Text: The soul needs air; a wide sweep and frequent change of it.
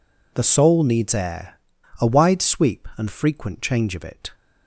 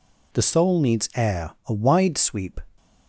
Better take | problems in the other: first | stops before "and frequent change of it"; at 2.7 s

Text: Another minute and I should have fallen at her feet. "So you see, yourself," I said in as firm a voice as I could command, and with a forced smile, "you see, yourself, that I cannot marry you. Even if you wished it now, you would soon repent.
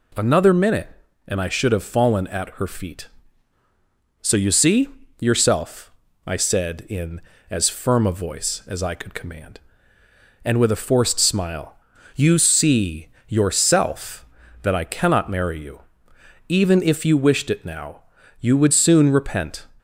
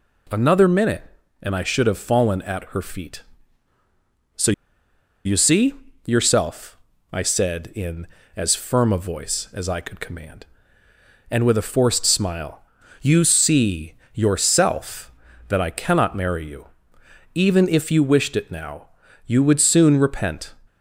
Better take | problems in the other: first | pauses between "So" and "you"; noticeable; at 4.5 s; 0.73 s long

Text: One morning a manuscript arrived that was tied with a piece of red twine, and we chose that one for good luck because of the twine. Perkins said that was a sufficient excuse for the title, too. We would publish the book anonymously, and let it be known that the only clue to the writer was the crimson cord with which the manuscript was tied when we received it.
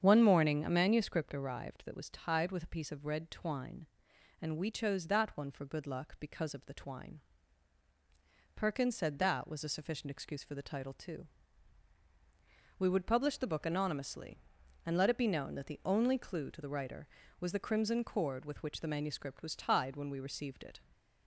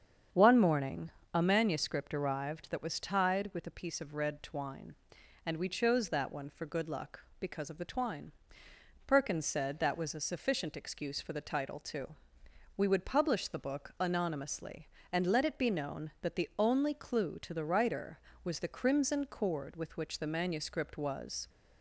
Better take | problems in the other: first | starts louder than the rest; strong; until 1.5 s; 7.5 dB; strong in the first // pauses between "morning" and "a"; slight; at 1.1 s; 0.24 s long // stops before "tied when we received it"; at 21.4 s

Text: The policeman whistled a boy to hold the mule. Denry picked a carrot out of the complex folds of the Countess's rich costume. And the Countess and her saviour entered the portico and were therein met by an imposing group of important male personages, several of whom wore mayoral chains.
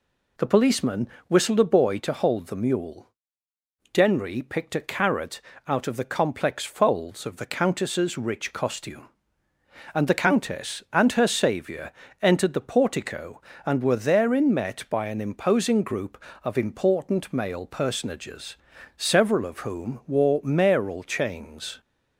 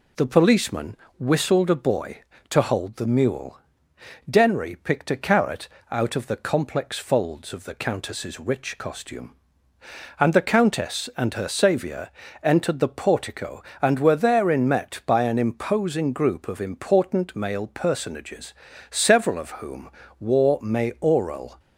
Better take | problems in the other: first | pauses between "policeman" and "whistled"; slight; at 0.9 s; 0.24 s long; slight in the first // pauses between "carrot" and "out"; slight; at 5.6 s; 0.24 s long; slight in the first // pauses between "saviour" and "entered"; slight; at 12.1 s; 0.32 s long; slight in the first // pauses between "whom" and "wore"; slight; at 19.9 s; 0.30 s long // stops before "chains"; at 21.5 s

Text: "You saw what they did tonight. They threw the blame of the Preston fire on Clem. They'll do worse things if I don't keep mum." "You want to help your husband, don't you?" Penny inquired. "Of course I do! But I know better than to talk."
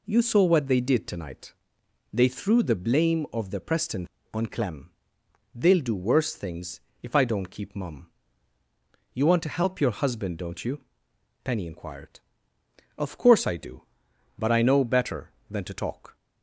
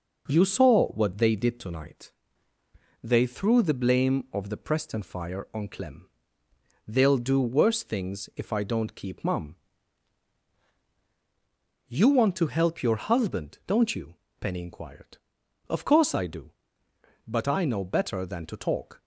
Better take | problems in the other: second | skips "fire"; at 4.1 s // pauses between "things" and "if"; slight; at 6.8 s; 0.20 s long

